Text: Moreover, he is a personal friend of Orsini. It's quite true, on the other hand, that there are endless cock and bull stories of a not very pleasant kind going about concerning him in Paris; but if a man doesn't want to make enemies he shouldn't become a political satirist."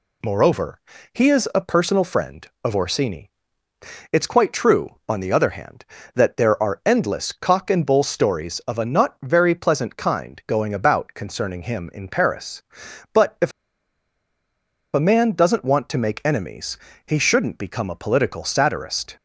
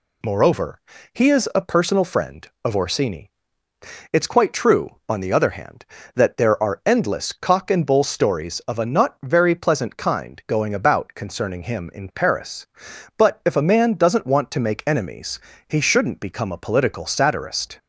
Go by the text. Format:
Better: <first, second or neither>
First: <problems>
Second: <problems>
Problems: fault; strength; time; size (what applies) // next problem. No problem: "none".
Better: second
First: pauses between "if" and "a"; strong; at 13.5 s; 1.4 s long // pauses between "enemies" and "he"; slight; at 16.7 s; 0.30 s long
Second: pauses between "enemies" and "he"; slight; at 15.3 s; 0.30 s long